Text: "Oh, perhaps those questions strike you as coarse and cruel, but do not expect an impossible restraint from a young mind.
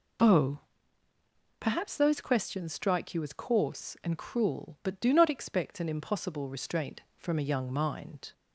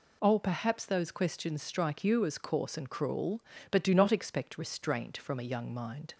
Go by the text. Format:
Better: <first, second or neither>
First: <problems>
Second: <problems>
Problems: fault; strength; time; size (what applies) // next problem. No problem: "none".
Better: first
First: none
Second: skips "an impossible"; at 4.5 s